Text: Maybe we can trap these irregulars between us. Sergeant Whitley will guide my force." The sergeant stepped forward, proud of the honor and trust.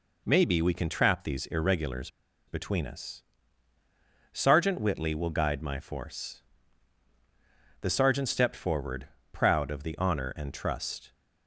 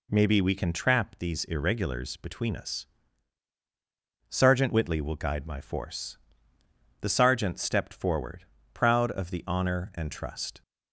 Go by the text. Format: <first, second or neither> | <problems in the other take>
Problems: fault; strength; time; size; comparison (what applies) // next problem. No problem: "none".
second | pauses between "irregulars" and "between"; at 2.0 s; 0.38 s long